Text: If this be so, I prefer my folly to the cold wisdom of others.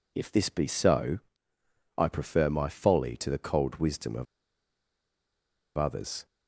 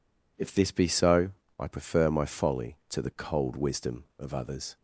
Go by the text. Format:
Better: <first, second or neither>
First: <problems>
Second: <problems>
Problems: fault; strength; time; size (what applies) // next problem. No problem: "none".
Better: second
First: pauses between "of" and "others"; strong; at 4.2 s; 1.5 s long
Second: none